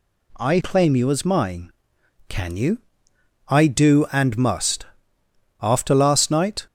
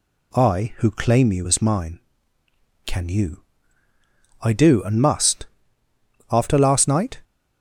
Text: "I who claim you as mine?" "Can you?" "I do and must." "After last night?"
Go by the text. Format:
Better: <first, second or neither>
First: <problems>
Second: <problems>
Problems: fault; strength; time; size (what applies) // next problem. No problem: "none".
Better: second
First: skips "who"; at 0.5 s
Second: none